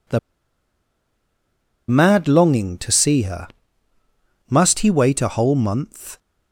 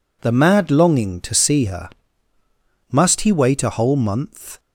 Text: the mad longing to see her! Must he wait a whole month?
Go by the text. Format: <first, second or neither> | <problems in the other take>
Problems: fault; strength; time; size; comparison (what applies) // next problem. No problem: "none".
second | pauses between "the" and "mad"; strong; at 0.1 s; 1.7 s long